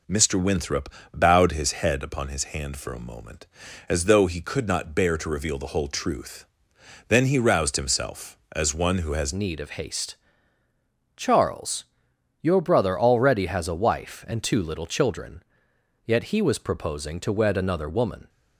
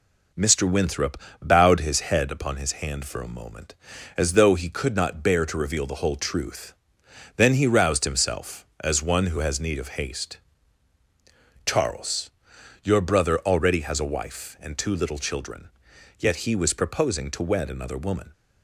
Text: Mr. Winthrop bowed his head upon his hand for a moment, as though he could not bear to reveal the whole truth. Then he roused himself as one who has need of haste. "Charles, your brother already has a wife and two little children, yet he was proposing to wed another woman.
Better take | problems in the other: second | pauses between "Winthrop" and "bowed"; slight; at 0.8 s; 0.24 s long; slight in the second // changes voice at "need"; from 9.3 s on; 8.9 s long

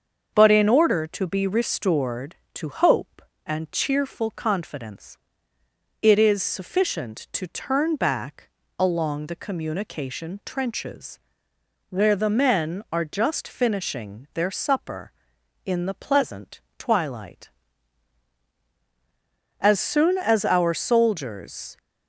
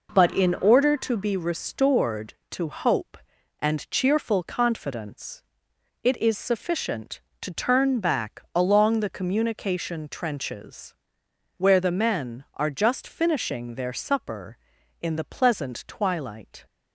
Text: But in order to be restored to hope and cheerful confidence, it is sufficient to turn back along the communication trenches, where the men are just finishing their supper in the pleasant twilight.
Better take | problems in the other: second | starts louder than the rest; until 1.3 s; 6.5 dB // pauses between "back" and "along"; slight; at 8.4 s; 0.30 s long // pauses between "pleasant" and "twilight"; slight; at 16.6 s; 0.16 s long // goes on to say "As soon as our soldiers"; strong; from 19.5 s on; 2.1 s long

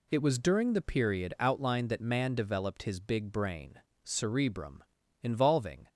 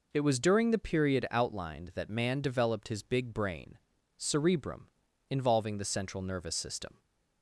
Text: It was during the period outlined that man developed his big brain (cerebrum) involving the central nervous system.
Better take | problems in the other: second | stops before "the central nervous system"; at 5.8 s

